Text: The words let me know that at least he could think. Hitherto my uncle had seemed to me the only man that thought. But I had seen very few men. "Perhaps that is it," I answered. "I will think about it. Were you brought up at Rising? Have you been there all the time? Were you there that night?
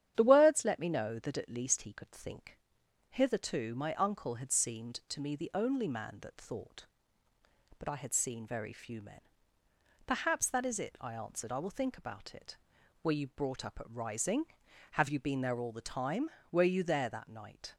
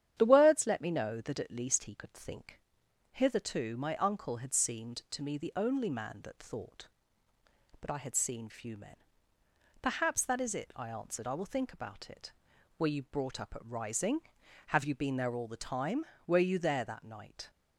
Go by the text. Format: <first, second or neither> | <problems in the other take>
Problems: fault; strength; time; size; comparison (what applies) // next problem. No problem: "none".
first | starts louder than the rest; strong; until 1.1 s; 9.5 dB; strong in the first // skips "very"; at 8.4 s